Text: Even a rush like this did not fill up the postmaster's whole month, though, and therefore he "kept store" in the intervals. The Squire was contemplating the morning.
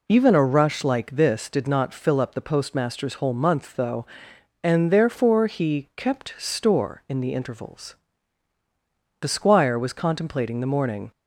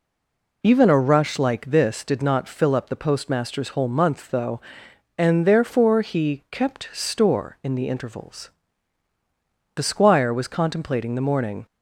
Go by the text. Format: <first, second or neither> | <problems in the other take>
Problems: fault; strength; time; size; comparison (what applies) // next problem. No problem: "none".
first | stays silent before the first word; slight; until 0.6 s; 0.6 s long